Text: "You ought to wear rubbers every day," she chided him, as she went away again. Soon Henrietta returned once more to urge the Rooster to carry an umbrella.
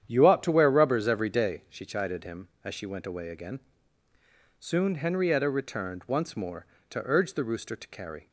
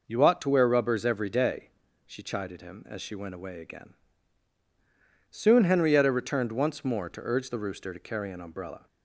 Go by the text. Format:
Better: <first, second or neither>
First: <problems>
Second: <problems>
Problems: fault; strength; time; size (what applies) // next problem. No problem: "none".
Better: second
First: starts louder than the rest; strong; until 1.0 s; 9.5 dB // stops before "an umbrella"; at 8.2 s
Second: none